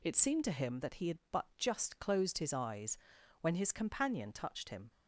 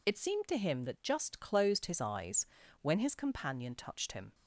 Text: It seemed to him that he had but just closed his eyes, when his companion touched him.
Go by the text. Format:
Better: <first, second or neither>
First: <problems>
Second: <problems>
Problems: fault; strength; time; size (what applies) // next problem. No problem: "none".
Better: first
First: none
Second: skips "he had but"; at 1.0 s